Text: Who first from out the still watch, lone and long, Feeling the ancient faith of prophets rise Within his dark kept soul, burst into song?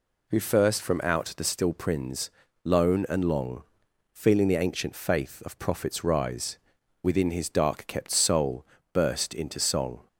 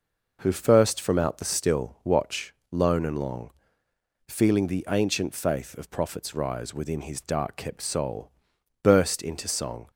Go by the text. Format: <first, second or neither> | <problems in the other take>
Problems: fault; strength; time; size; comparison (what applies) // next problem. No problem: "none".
second | says "prins" for "watch"; at 1.7 s // pauses between "rise" and "Within"; at 6.5 s; 0.44 s long